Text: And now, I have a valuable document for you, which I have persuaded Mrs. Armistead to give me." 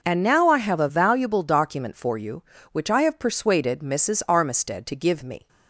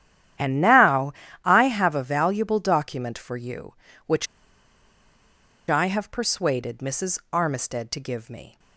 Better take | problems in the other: first | starts louder than the rest; strong; until 1.7 s; 10.5 dB // pauses between "which" and "I"; strong; at 4.2 s; 1.4 s long

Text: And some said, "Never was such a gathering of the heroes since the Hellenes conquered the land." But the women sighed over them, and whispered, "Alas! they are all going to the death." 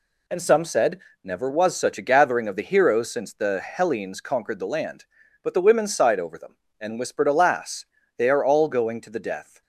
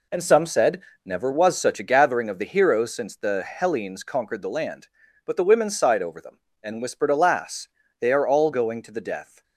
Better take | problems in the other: first | starts louder than the rest; slight; until 2.0 s; 3 dB

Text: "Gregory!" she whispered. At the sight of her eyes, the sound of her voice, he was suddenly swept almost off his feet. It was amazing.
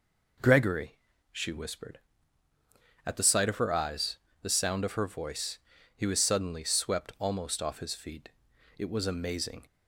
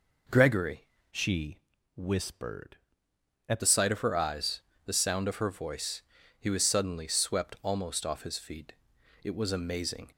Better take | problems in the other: first | changes voice from "she" to "At"; from 1.1 to 3.6 s; 2.5 s long // pauses between "she" and "whispered"; slight; at 1.5 s; 0.36 s long

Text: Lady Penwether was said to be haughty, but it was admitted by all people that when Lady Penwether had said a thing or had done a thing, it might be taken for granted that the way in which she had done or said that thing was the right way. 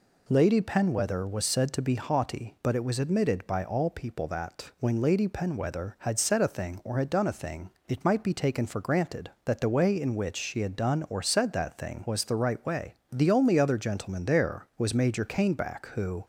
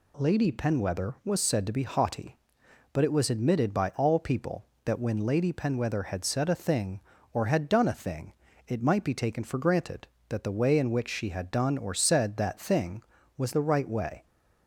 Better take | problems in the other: second | goes on to say "The only other gentleman there was Major Caneback who"; strong; from 13.1 s on; 3.1 s long

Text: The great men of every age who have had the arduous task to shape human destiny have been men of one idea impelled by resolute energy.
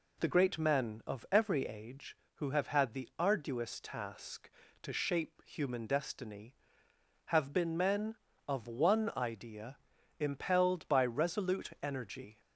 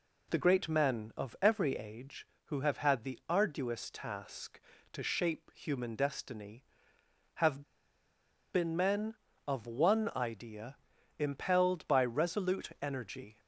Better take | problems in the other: first | pauses between "have" and "been"; noticeable; at 7.6 s; 0.91 s long // pauses between "idea" and "impelled"; at 10.7 s; 0.42 s long; also in the first

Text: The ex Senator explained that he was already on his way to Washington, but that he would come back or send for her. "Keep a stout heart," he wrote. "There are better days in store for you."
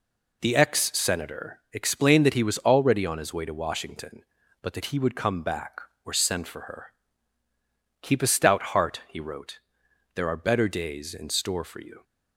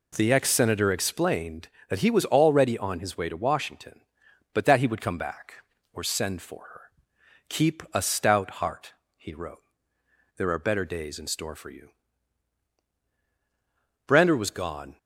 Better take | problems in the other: first | goes on to say "Brander was gone"; noticeable; from 14.0 s on; 0.92 s long

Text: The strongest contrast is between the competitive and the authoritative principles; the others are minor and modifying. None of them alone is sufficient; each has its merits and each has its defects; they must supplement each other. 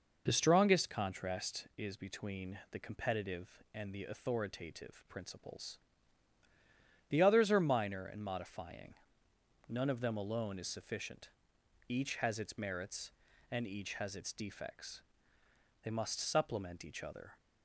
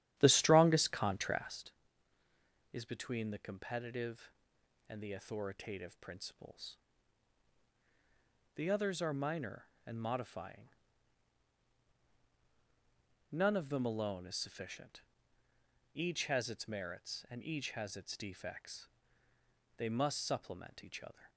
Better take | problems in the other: first | starts louder than the rest; strong; until 1.7 s; 11.5 dB

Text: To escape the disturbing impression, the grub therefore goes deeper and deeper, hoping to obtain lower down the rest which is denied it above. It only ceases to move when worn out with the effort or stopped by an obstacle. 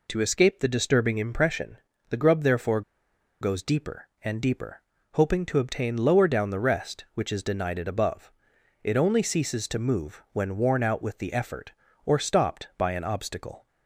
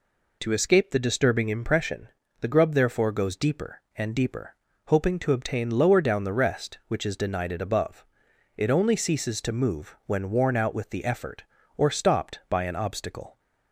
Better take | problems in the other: second | pauses between "therefore" and "goes"; noticeable; at 2.8 s; 0.60 s long

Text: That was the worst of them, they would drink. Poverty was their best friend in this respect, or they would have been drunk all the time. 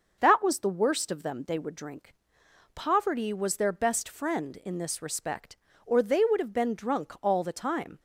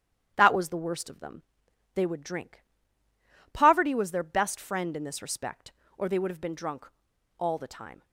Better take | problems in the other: first | starts louder than the rest; strong; until 1.3 s; 10 dB // pauses between "drunk" and "all"; noticeable; at 6.8 s; 0.50 s long

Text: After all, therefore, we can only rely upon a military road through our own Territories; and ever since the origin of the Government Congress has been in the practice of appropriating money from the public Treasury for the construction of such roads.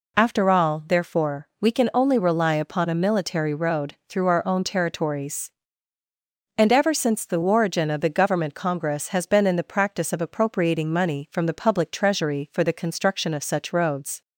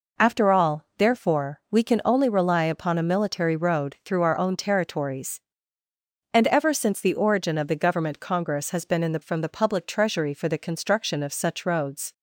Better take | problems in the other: first | skips "practice of appropriating money"; at 9.2 s

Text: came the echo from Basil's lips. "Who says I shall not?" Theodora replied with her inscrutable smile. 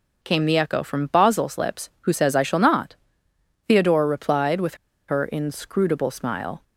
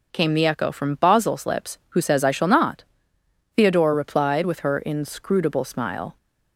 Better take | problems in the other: second | pauses between "with" and "her"; slight; at 4.7 s; 0.32 s long

